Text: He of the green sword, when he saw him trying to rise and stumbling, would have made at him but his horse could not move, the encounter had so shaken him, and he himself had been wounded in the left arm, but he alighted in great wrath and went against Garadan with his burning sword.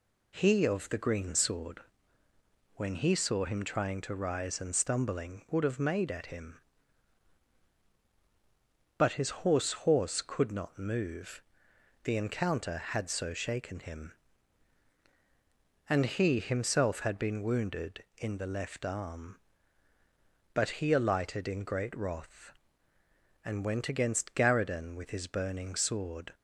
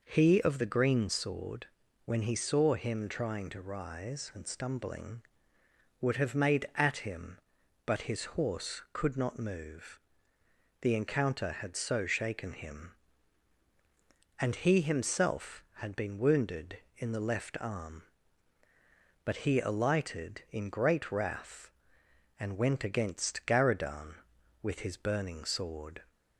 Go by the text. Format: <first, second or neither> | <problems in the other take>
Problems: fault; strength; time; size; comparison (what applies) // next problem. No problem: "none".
second | says "horse" twice; at 9.7 s